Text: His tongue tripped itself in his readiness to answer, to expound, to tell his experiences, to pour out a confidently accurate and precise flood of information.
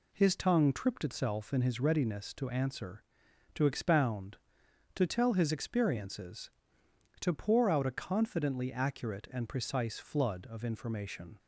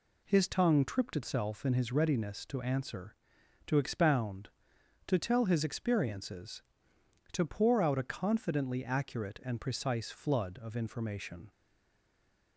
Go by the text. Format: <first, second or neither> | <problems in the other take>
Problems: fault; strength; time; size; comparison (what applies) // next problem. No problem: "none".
first | stays silent after the last word; from 11.5 s on; 1.0 s long